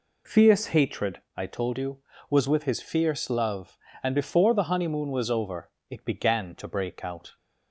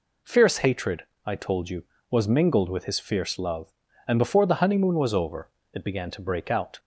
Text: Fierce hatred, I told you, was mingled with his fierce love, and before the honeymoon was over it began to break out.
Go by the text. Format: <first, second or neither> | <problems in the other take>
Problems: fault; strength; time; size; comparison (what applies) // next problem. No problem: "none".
second | skips "mingled"; at 2.4 s // pauses between "over" and "it"; slight; at 5.7 s; 0.18 s long; slight in the second